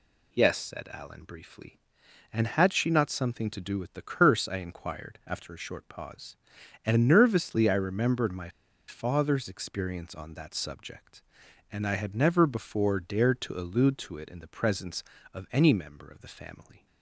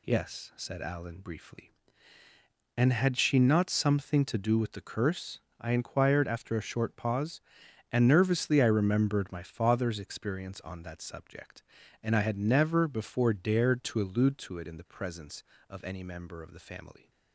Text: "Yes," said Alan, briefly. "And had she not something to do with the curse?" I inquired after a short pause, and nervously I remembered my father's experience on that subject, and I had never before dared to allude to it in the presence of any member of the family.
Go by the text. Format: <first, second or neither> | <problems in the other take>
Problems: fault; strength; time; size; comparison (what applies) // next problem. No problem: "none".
second | pauses between "my" and "father's"; at 8.4 s; 0.39 s long